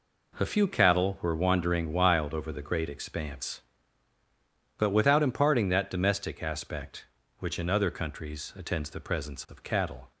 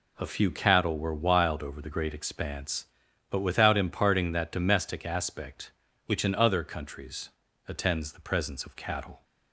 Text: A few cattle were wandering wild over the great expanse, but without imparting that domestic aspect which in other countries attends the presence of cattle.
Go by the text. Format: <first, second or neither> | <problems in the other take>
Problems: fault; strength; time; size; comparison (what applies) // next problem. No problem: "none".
first | skips "wandering"; at 1.1 s // pauses between "countries" and "attends"; slight; at 7.3 s; 0.36 s long